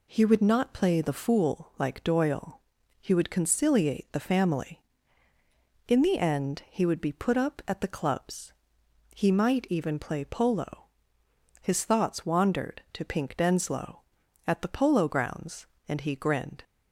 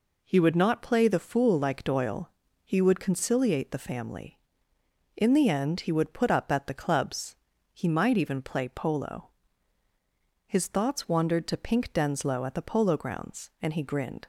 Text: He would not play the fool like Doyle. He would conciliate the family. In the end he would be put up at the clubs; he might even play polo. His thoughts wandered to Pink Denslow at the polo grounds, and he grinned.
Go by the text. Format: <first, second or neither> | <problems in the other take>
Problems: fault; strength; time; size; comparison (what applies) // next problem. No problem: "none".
first | skips "be"; at 6.1 s